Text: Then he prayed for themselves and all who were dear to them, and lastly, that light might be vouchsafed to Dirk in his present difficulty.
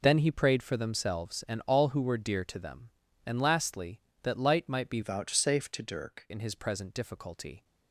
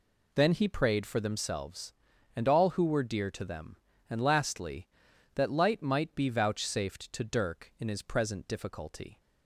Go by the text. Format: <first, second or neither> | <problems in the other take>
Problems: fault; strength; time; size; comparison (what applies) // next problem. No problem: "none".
second | changes voice from "vouchsafed" to "Dirk"; from 5.0 to 6.2 s; 1.2 s long